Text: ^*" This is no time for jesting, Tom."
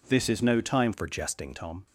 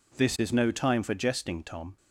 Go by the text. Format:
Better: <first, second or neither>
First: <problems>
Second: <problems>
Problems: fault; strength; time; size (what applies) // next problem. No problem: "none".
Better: second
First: changes voice from "for" to "jesting"; from 0.9 to 1.5 s; 0.6 s long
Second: none